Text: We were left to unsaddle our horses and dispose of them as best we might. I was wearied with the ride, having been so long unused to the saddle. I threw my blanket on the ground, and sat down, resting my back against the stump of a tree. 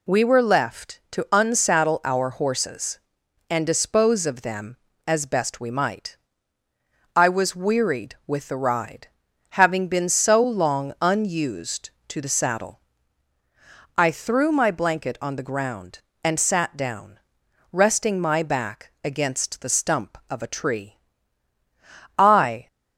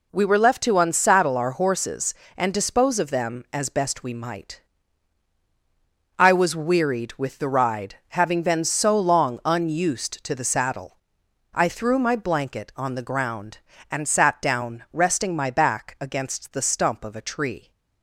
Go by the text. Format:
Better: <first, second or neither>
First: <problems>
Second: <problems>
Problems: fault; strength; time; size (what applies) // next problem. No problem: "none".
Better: second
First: goes on to say "I"; slight; from 22.1 s on; 0.48 s long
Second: none